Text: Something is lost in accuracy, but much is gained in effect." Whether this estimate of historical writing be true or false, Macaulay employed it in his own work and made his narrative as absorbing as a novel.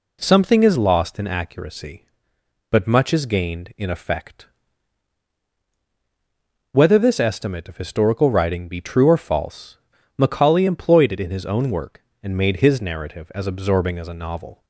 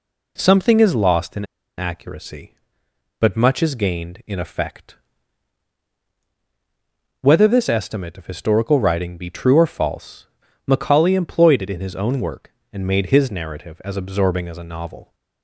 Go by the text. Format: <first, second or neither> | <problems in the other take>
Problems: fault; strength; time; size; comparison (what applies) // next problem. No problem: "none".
first | pauses between "in" and "accuracy"; slight; at 1.4 s; 0.32 s long